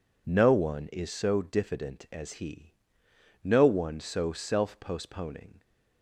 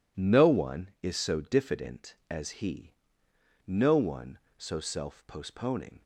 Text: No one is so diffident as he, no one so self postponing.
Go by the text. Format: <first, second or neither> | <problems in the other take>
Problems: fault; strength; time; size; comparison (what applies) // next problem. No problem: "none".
neither | none